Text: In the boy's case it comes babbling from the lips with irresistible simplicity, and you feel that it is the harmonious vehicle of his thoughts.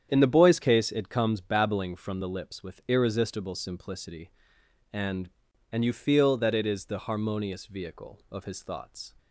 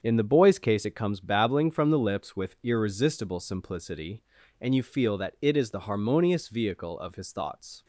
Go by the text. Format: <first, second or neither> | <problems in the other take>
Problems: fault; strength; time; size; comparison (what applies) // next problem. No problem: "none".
second | starts louder than the rest; strong; until 1.1 s; 8.5 dB; strong in the second // says "and" twice; at 5.7 s